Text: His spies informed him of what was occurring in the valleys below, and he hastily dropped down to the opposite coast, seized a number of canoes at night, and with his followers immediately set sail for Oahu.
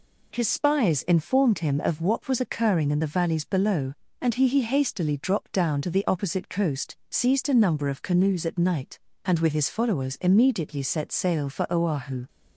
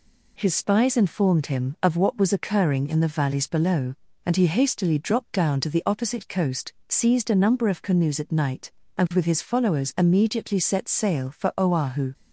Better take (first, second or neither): second